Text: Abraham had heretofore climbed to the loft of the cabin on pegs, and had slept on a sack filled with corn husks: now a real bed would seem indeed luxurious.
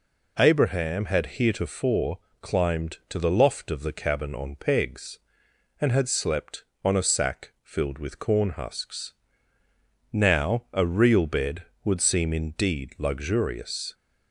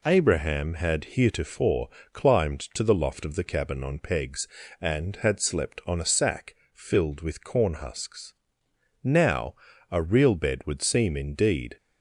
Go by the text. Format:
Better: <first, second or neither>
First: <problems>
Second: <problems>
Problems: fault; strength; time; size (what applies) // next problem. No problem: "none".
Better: first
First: pauses between "heretofore" and "climbed"; slight; at 2.1 s; 0.22 s long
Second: pauses between "heretofore" and "climbed"; slight; at 1.8 s; 0.24 s long // pauses between "sack" and "filled"; slight; at 6.5 s; 0.18 s long // pauses between "now" and "a"; at 9.5 s; 0.38 s long // stops before "luxurious"; at 11.7 s